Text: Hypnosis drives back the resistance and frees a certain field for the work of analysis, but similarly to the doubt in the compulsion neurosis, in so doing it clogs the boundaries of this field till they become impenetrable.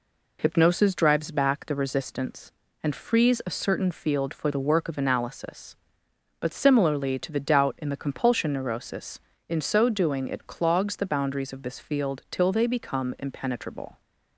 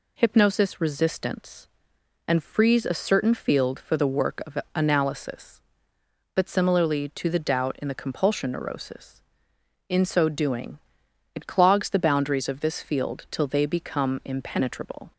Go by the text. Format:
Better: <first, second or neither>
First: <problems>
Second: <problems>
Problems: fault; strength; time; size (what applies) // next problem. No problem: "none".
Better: first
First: none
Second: skips "drives back the"; at 0.7 s // pauses between "of" and "analysis"; slight; at 4.5 s; 0.18 s long // pauses between "doing" and "it"; noticeable; at 10.7 s; 0.56 s long